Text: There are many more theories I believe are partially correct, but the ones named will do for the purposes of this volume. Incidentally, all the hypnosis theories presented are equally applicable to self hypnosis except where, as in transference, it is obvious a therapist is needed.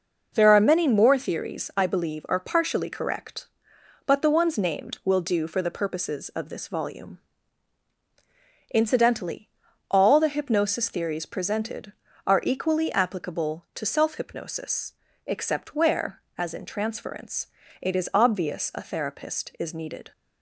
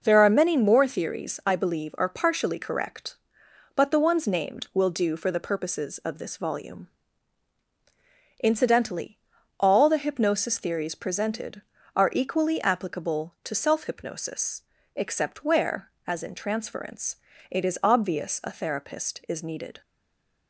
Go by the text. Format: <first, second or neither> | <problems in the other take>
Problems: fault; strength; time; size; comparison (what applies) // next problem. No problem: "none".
first | pauses between "hypnosis" and "except"; slight; at 14.6 s; 0.32 s long; slight in the first // stays silent after the last word; slight; from 19.8 s on; 0.6 s long